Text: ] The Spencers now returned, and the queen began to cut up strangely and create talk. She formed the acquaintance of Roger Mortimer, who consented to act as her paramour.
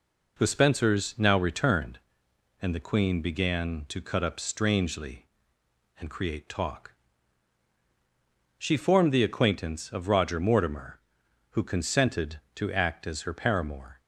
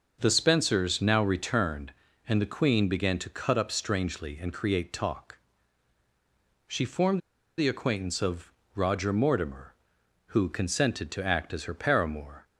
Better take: first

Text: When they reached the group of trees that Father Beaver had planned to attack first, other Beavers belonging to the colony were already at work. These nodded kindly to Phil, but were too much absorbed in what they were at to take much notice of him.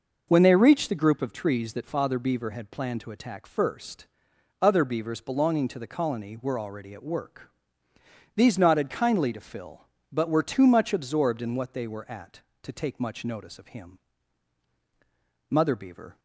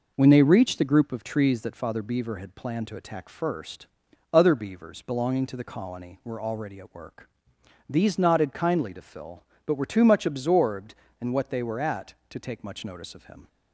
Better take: second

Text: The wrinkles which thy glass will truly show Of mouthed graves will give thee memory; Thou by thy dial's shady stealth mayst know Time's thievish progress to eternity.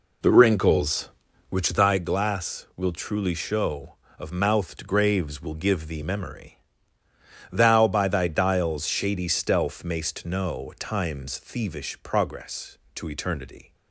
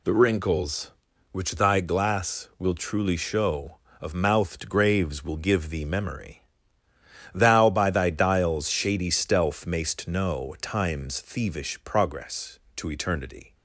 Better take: second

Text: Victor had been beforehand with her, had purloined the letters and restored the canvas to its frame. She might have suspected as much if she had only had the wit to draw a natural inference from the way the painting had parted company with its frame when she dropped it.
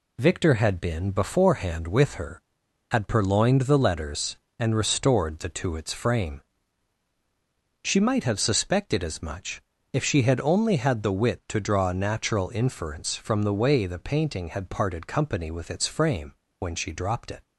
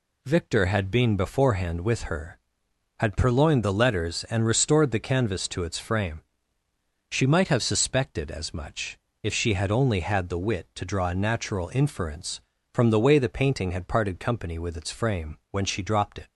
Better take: second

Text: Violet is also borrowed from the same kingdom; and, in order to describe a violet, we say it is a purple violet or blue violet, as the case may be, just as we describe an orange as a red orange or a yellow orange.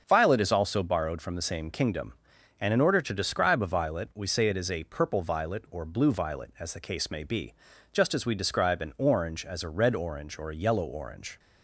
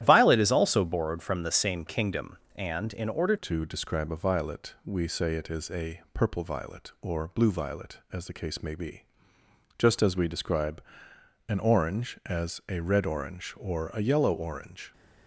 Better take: first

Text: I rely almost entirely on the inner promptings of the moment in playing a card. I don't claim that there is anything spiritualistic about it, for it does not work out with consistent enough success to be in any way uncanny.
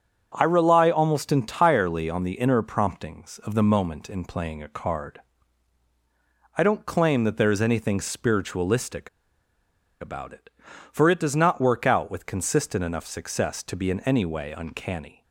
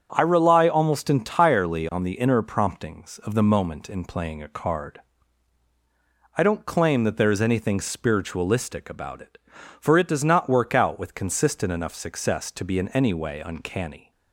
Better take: second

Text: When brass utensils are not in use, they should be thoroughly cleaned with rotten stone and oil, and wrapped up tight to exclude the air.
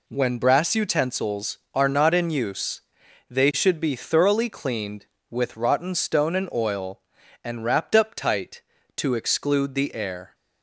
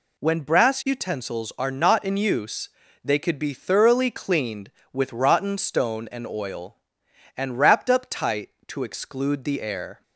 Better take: first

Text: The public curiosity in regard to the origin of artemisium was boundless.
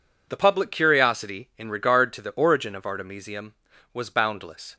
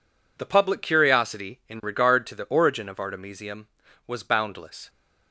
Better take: neither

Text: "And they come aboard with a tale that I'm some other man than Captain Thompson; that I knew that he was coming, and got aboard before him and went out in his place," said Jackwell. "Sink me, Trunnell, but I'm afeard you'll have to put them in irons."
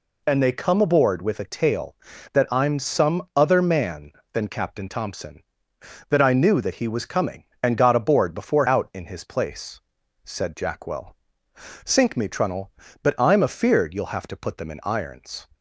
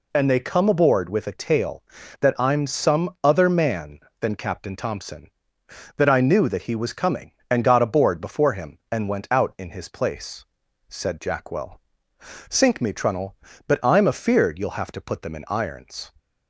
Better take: second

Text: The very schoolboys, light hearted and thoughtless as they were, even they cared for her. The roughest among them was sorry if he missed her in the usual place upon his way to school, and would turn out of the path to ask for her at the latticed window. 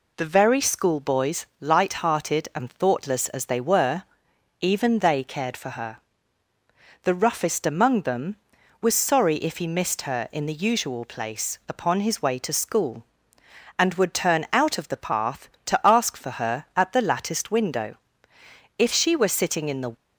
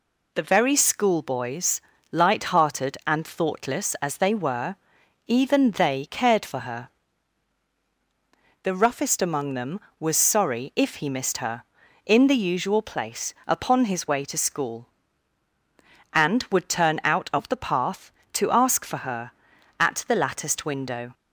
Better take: second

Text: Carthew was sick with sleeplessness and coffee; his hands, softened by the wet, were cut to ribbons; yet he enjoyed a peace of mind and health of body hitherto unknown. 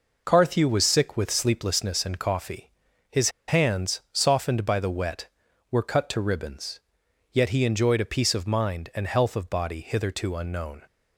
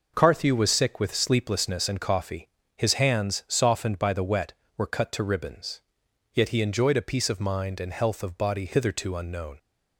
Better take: second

